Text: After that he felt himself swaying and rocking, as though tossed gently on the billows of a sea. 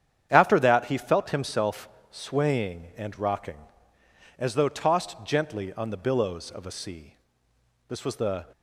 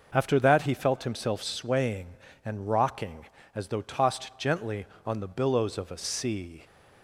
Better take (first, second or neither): second